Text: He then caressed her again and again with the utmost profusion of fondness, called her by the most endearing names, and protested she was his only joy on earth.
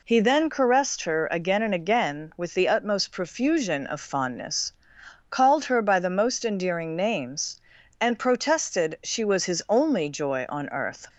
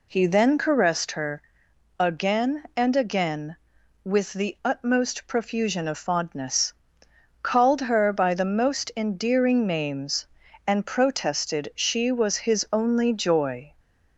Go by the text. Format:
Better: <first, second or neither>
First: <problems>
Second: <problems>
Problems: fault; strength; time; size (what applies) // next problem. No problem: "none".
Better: first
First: none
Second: pauses between "her" and "again"; noticeable; at 1.3 s; 0.60 s long // stops before "on earth"; at 13.7 s